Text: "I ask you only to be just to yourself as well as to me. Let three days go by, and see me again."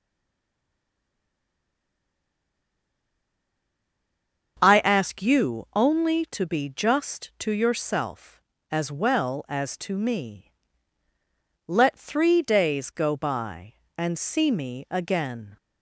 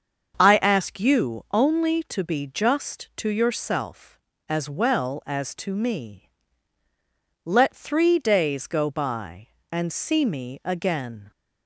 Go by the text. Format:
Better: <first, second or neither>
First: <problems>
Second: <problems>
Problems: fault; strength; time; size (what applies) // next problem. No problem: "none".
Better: second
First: stays silent before the first word; strong; until 4.5 s; 4.5 s long // starts louder than the rest; until 5.6 s; 6.5 dB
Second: starts louder than the rest; until 1.4 s; 6.5 dB